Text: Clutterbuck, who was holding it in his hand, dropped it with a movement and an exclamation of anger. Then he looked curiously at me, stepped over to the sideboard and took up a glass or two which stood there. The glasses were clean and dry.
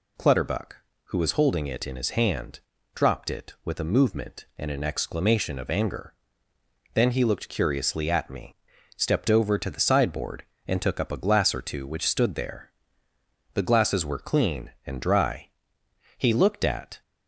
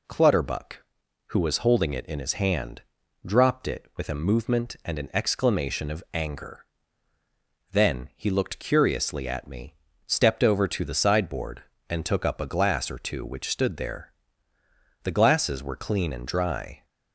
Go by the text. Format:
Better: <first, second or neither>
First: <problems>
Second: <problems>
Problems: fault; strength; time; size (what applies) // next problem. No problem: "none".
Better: second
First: goes on to say "He looked at"; noticeable; from 16.1 s on; 0.84 s long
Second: none